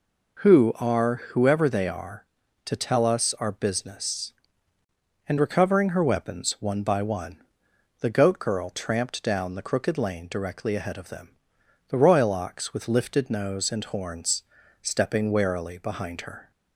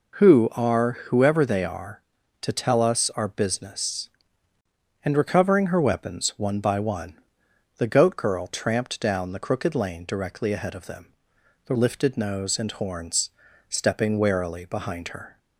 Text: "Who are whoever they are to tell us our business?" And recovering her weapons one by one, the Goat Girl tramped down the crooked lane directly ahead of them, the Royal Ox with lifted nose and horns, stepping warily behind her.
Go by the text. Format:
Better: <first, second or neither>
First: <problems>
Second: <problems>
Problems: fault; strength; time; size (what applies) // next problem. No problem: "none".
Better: first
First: none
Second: skips "Royal Ox with"; at 11.7 s